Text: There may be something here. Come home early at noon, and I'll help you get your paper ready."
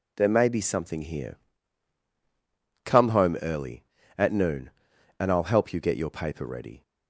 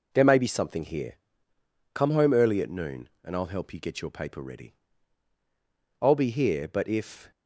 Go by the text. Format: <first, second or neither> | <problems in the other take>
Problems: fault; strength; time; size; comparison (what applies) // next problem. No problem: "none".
first | goes on to say "I'll be here but if"; noticeable; from 6.0 s on; 1.3 s long